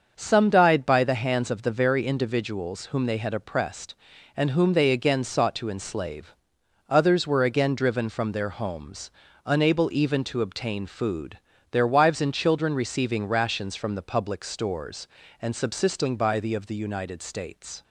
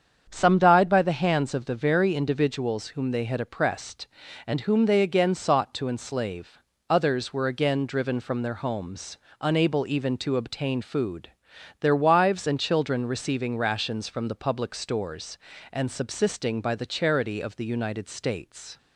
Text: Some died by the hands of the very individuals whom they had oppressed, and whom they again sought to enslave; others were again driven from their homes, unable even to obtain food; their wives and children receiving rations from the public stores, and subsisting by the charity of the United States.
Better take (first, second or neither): second